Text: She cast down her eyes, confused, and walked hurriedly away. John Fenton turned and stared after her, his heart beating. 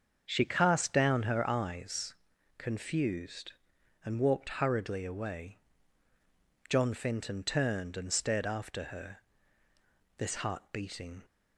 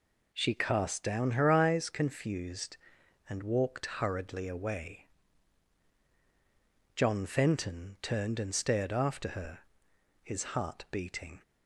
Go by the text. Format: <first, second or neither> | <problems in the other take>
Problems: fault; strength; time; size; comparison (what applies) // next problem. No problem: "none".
second | starts louder than the rest; until 1.2 s; 7 dB // says "this" for "his"; at 10.1 s